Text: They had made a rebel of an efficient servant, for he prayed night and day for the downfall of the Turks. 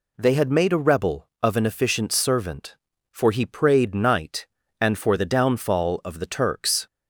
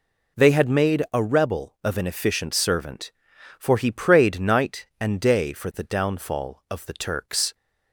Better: second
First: skips "day"; at 4.9 s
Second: none

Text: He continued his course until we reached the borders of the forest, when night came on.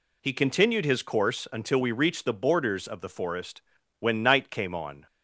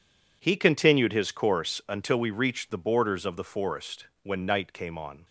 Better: first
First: none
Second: gets quieter; strong; throughout; 14.5 dB

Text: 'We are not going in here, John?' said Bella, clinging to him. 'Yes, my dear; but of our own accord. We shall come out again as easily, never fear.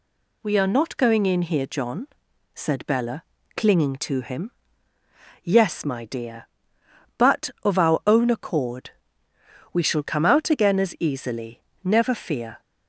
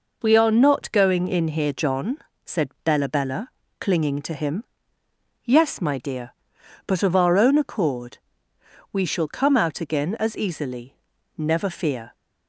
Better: first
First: none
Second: says "Bella" twice; at 3.0 s

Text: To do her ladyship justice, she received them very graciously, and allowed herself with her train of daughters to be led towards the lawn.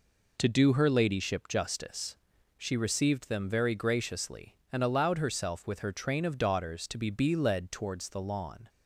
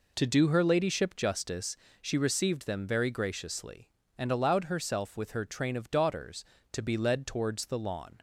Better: second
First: says "be" twice; at 7.0 s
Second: none

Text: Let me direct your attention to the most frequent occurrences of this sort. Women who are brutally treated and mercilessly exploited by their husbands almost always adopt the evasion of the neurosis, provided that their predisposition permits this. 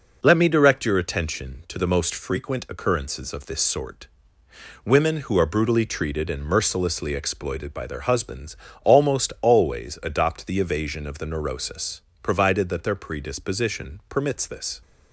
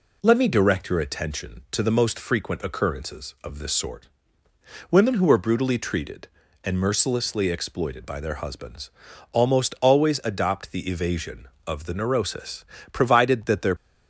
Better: first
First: pauses between "husbands" and "almost"; slight; at 8.5 s; 0.28 s long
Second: pauses between "husbands" and "almost"; at 8.9 s; 0.42 s long // stops before "predisposition permits this"; at 13.7 s

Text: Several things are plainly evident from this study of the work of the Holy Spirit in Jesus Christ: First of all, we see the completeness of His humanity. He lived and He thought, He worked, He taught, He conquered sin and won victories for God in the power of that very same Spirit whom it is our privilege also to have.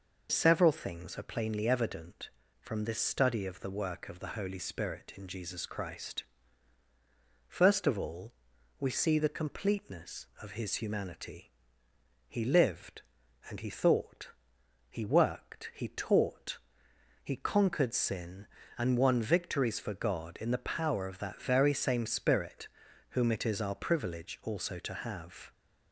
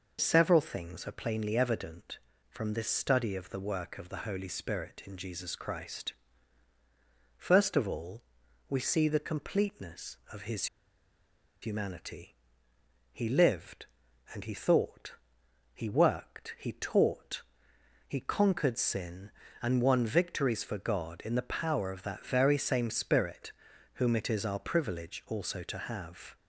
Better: first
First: pauses between "Spirit" and "whom"; at 22.6 s; 0.42 s long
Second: pauses between "His" and "humanity"; noticeable; at 10.6 s; 0.96 s long // pauses between "Spirit" and "whom"; at 23.5 s; 0.42 s long

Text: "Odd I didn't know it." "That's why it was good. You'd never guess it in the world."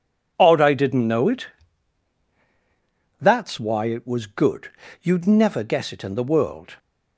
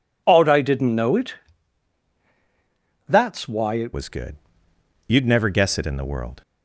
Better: first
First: none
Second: changes voice at "was"; from 3.9 s on; 2.5 s long

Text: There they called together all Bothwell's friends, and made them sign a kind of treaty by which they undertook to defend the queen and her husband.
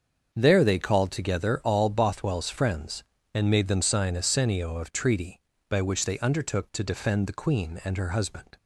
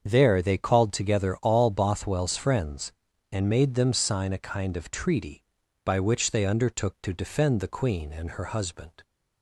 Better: second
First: starts louder than the rest; until 1.3 s; 7 dB // says "senio" for "kind"; at 4.2 s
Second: starts louder than the rest; until 1.0 s; 7 dB

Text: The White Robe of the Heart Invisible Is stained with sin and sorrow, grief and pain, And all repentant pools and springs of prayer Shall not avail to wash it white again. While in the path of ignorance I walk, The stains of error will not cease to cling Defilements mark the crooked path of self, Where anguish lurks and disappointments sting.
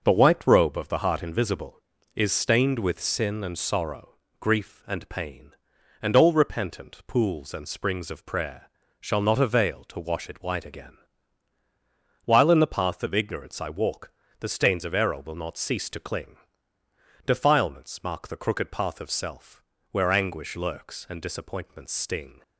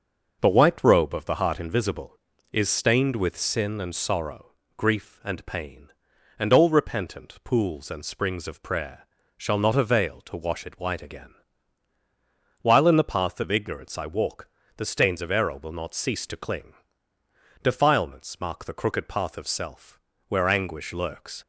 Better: first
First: starts louder than the rest; until 1.0 s; 6 dB // pauses between "prayer" and "Shall"; slight; at 8.6 s; 0.32 s long // pauses between "cling" and "Defilements"; noticeable; at 16.3 s; 0.90 s long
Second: starts louder than the rest; until 1.4 s; 6 dB // pauses between "prayer" and "Shall"; slight; at 9.0 s; 0.32 s long // pauses between "cling" and "Defilements"; noticeable; at 16.7 s; 0.90 s long // stops before "and disappointments sting"; at 21.4 s

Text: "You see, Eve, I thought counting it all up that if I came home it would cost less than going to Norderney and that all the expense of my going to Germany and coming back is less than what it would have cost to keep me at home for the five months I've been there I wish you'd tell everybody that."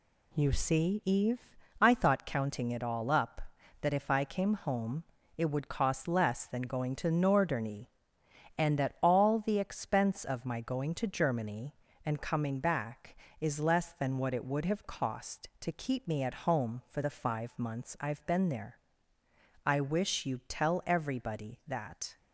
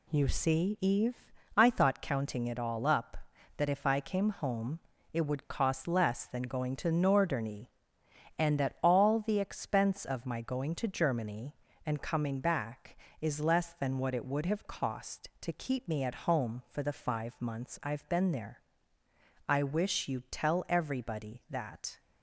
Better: neither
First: pauses between "home" and "it"; slight; at 5.0 s; 0.32 s long // pauses between "there" and "I"; noticeable; at 18.7 s; 0.88 s long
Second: pauses between "home" and "it"; slight; at 4.8 s; 0.32 s long // pauses between "there" and "I"; noticeable; at 18.6 s; 0.88 s long

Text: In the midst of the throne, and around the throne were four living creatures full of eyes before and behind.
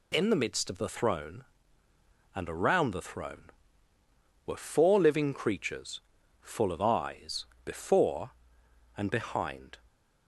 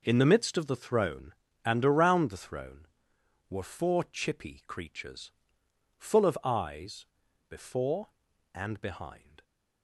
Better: first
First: pauses between "creatures" and "full"; at 6.0 s; 0.42 s long // pauses between "eyes" and "before"; slight; at 7.4 s; 0.18 s long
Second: says "chippy" for "living"; at 4.0 s // pauses between "creatures" and "full"; noticeable; at 5.3 s; 0.66 s long // pauses between "eyes" and "before"; at 7.0 s; 0.44 s long

